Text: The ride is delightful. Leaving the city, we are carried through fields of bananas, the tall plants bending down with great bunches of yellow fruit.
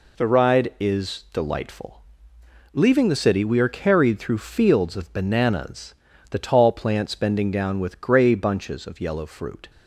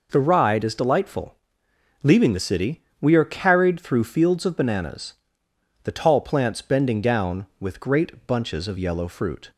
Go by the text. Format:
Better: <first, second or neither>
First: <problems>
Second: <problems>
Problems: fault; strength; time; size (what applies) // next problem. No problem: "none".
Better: second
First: says "grey" for "great"; at 8.0 s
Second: none